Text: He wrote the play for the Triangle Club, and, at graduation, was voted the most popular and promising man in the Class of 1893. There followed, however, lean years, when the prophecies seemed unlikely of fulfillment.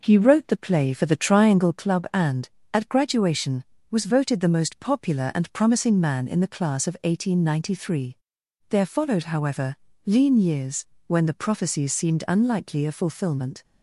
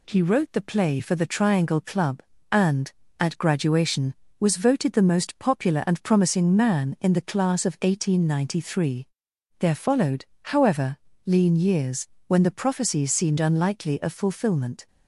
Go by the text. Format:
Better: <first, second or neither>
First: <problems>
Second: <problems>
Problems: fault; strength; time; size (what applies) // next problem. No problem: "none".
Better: second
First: starts louder than the rest; noticeable; until 1.8 s; 5 dB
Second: none